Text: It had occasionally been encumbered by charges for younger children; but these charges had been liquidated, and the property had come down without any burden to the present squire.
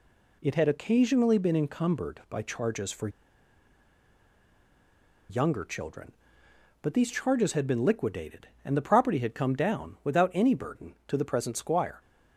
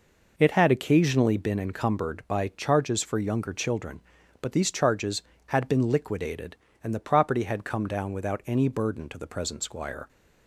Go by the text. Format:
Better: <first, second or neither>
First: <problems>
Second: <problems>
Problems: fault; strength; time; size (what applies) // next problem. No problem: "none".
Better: second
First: pauses between "for" and "younger"; strong; at 3.0 s; 2.2 s long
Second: none